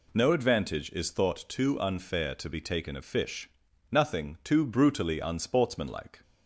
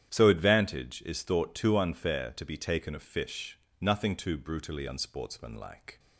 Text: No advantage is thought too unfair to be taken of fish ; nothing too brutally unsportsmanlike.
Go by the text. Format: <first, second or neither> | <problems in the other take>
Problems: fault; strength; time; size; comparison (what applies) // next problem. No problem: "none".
first | starts louder than the rest; strong; until 1.1 s; 10 dB // says "So" for "No"; at 0.1 s